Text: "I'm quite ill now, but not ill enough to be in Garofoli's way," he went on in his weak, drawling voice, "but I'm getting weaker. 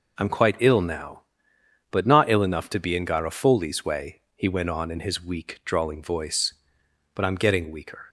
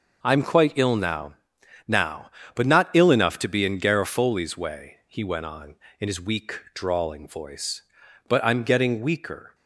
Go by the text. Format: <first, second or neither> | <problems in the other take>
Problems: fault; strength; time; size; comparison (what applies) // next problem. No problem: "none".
first | says "now" twice; at 1.8 s